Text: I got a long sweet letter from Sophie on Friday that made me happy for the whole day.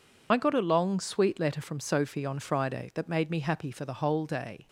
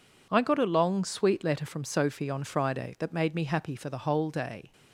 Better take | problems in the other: second | loses the start of "I"; at 0.3 s; 45 ms

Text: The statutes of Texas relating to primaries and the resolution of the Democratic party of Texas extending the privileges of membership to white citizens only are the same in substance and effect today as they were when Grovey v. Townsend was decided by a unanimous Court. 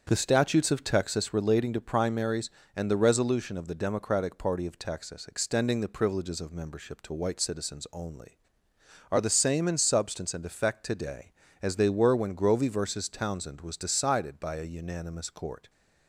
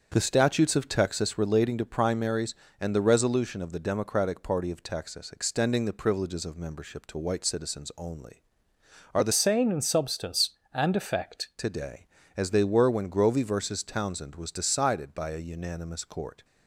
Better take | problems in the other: first | starts louder than the rest; strong; until 1.1 s; 7 dB; strong in the first // changes voice from "same" to "effect"; from 9.3 to 11.4 s; 2.1 s long

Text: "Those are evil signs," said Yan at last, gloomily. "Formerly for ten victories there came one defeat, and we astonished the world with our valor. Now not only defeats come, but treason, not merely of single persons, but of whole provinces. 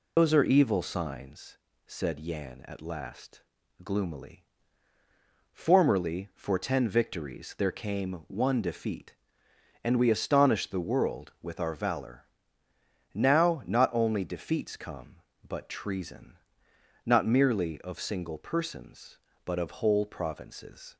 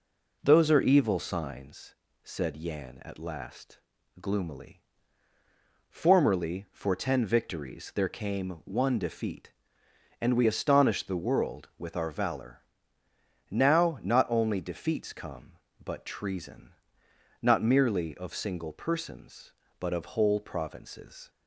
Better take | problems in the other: second | loses the start of "Those"; at 0.1 s; 125 ms

